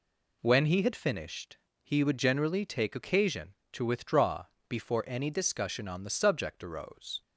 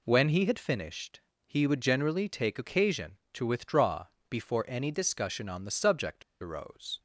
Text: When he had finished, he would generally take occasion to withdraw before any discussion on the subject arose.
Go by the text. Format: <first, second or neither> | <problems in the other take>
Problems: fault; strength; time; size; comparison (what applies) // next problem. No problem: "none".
first | pauses between "withdraw" and "before"; slight; at 4.0 s; 0.24 s long; slight in the first // pauses between "subject" and "arose"; slight; at 6.2 s; 0.18 s long